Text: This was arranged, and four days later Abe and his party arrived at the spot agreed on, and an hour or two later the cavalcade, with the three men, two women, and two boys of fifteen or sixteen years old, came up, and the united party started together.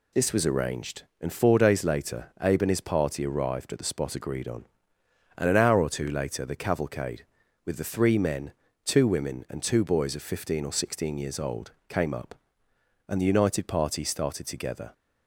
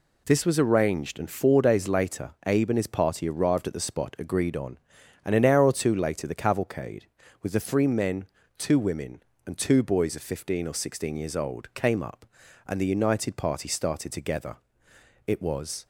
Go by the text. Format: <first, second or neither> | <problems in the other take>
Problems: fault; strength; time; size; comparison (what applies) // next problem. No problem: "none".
first | pauses between "later" and "Abe"; slight; at 2.2 s; 0.16 s long // goes on to say "It was"; from 15.2 s on; 0.58 s long